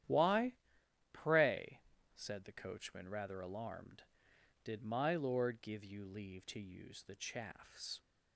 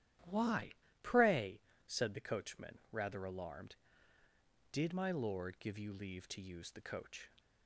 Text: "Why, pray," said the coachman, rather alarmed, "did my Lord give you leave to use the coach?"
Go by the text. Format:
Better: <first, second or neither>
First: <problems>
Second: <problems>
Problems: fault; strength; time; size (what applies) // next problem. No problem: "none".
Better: second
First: starts louder than the rest; strong; until 1.6 s; 11 dB // says "chaffs" for "coach"; at 7.1 s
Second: starts louder than the rest; strong; until 1.5 s; 12 dB